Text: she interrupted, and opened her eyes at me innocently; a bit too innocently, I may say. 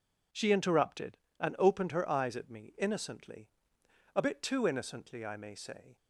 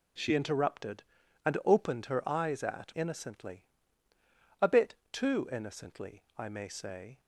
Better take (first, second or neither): first